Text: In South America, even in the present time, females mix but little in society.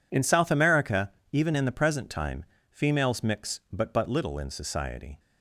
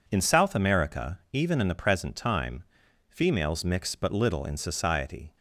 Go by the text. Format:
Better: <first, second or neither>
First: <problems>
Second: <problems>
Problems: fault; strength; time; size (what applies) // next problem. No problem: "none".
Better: second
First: says "but" twice; at 3.9 s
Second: none